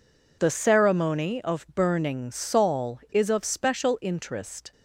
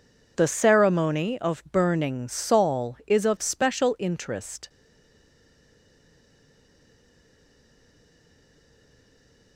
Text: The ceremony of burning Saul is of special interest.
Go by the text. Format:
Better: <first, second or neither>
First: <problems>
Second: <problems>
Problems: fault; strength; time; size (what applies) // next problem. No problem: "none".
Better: first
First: none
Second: stays silent after the last word; strong; from 4.6 s on; 4.9 s long